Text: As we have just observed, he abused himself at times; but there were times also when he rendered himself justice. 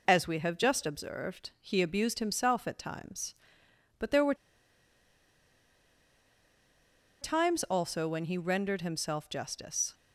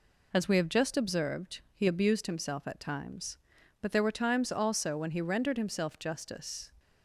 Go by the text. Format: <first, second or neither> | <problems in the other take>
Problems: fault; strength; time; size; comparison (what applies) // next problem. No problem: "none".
second | pauses between "were" and "times"; strong; at 4.3 s; 2.8 s long